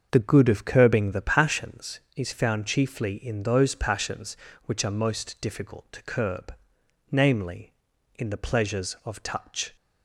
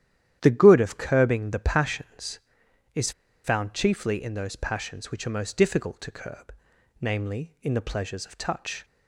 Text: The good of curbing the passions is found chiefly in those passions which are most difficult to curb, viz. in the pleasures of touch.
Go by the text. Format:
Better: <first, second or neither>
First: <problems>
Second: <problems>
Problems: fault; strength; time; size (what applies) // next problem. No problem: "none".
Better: first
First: starts louder than the rest; until 1.1 s; 6.5 dB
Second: starts louder than the rest; strong; until 1.4 s; 11 dB // pauses between "is" and "found"; slight; at 3.1 s; 0.32 s long